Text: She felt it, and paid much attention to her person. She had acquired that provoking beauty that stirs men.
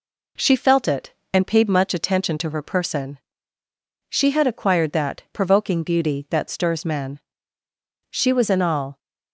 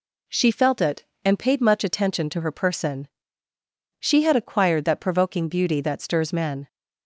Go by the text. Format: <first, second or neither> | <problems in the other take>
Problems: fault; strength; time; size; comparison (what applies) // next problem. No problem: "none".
second | goes on to say "She was in all"; noticeable; from 8.1 s on; 0.88 s long